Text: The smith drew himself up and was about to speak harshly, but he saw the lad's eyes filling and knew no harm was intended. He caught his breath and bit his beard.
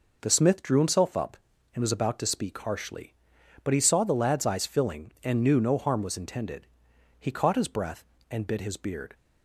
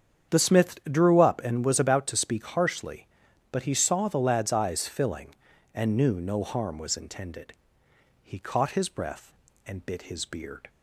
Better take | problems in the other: first | starts louder than the rest; strong; until 1.4 s; 8.5 dB // skips "himself"; at 1.2 s

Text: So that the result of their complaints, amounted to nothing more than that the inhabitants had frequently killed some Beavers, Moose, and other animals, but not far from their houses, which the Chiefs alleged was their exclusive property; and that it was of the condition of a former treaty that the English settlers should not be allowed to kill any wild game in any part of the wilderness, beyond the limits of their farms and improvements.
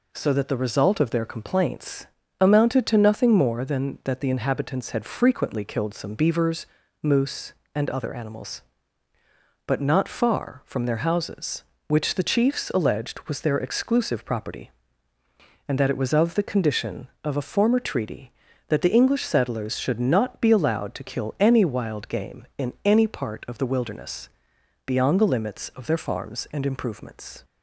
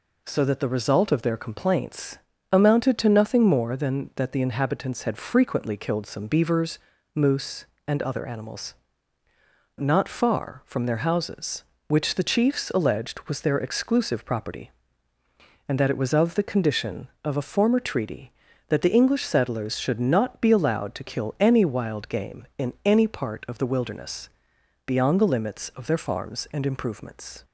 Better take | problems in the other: first | skips "but"; at 9.2 s

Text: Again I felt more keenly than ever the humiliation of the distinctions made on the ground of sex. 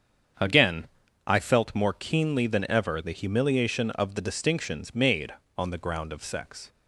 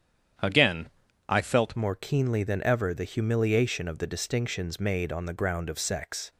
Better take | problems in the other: first | starts louder than the rest; strong; until 1.7 s; 9 dB; strong in the first // pauses between "Again" and "I"; at 0.8 s; 0.38 s long; also in the first // changes voice at "more"; from 1.7 s on; 4.6 s long

